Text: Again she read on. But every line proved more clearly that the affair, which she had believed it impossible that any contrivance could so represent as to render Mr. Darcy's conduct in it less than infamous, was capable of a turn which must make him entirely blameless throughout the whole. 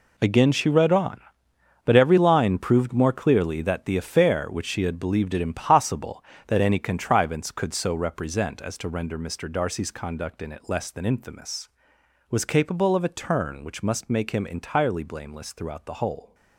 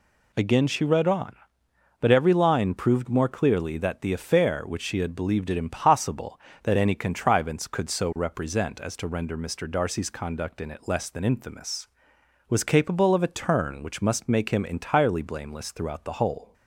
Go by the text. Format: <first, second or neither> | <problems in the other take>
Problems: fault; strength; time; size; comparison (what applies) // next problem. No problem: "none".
second | gets quieter; strong; throughout; 12.5 dB